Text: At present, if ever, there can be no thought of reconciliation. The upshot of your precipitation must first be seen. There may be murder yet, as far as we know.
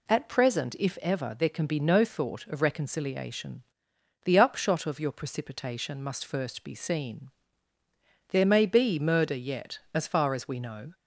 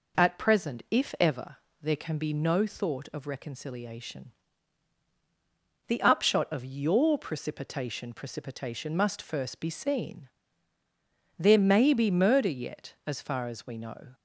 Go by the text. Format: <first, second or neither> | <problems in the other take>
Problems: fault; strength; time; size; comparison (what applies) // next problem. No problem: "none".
first | says "precipitation" twice; at 8.1 s